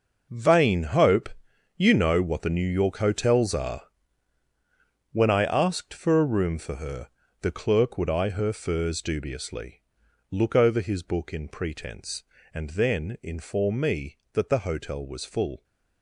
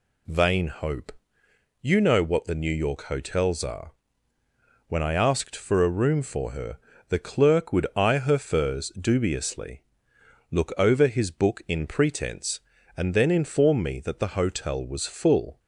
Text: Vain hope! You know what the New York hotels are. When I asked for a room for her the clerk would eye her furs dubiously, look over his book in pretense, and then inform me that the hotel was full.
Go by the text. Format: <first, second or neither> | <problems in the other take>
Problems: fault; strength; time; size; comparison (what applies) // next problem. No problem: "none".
second | gets quieter; strong; throughout; 12.5 dB // pauses between "her" and "the"; slight; at 7.0 s; 0.32 s long; slight in the second